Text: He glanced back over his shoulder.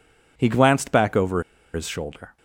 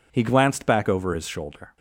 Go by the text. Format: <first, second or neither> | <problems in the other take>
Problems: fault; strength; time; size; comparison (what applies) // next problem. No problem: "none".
second | pauses between "over" and "his"; slight; at 1.4 s; 0.32 s long